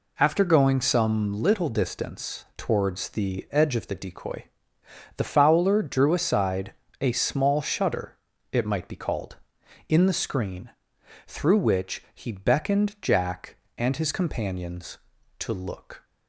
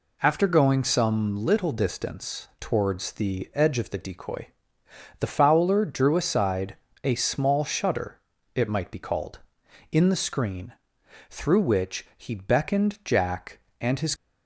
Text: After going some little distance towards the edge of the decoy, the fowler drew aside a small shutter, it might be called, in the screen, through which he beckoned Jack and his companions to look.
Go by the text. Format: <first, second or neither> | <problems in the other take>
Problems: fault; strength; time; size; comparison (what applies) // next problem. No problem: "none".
first | pauses between "aside" and "a"; slight; at 6.7 s; 0.28 s long; slight in the first // stops before "companions to look"; at 14.1 s